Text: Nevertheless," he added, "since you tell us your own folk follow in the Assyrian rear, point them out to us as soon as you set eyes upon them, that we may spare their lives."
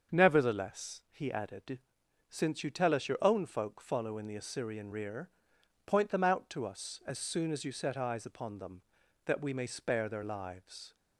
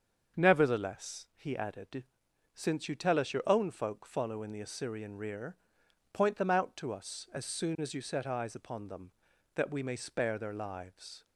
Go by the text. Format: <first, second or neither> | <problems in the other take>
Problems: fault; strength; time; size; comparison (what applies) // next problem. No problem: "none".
neither | starts louder than the rest; the same in both